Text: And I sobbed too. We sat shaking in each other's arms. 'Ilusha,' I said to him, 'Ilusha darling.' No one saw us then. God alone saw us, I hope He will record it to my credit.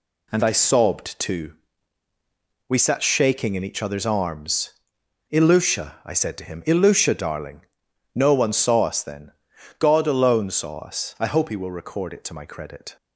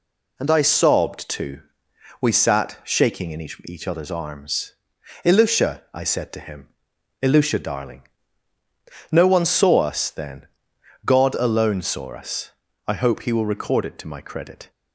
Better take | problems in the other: first | says "each" twice; at 3.6 s

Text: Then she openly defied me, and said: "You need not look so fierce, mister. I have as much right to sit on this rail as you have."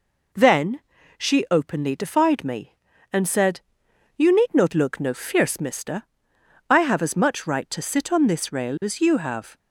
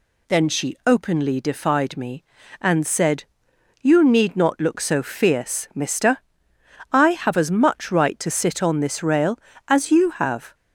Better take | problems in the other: second | pauses between "Then" and "she"; at 0.7 s; 0.38 s long // says "no" for "so"; at 4.9 s

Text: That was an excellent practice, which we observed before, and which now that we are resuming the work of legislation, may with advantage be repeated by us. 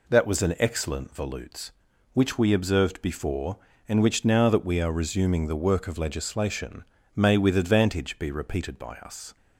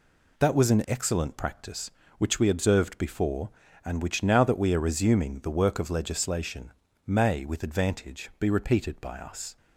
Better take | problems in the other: second | says "volutes" for "practice"; at 1.1 s

